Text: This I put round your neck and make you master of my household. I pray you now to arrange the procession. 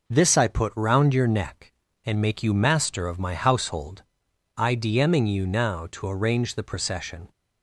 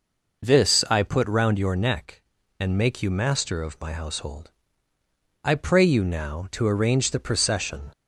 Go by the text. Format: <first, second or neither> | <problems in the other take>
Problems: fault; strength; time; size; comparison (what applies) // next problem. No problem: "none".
second | says "dming" for "pray"; at 4.7 s